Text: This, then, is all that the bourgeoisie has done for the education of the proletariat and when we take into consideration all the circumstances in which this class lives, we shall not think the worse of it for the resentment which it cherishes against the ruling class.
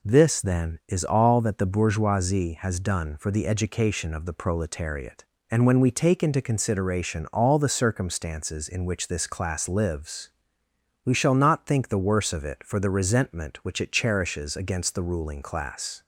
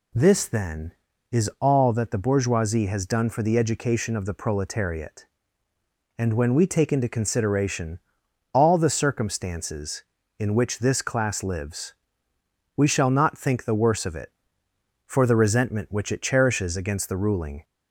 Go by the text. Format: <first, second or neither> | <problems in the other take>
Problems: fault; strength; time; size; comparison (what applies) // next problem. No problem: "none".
first | pauses between "consideration" and "all"; noticeable; at 7.9 s; 0.56 s long // stops before "class"; at 17.6 s